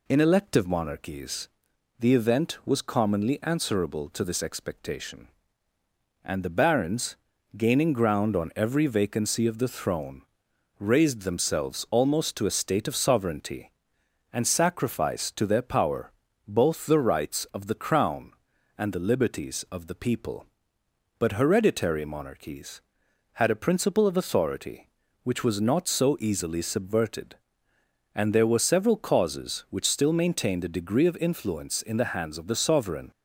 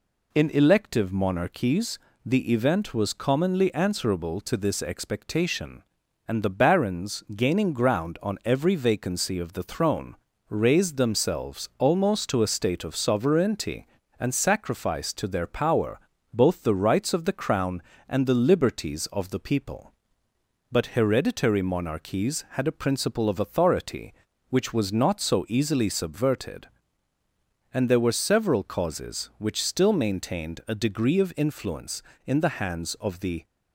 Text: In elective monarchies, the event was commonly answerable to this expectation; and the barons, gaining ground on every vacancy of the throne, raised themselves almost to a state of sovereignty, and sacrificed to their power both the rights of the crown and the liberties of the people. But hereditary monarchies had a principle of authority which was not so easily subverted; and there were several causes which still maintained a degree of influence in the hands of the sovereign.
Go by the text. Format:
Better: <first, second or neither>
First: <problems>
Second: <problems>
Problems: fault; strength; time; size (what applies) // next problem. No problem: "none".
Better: first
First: pauses between "power" and "both"; slight; at 16.1 s; 0.36 s long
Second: pauses between "power" and "both"; slight; at 15.9 s; 0.34 s long // stops before "sovereign"; at 33.4 s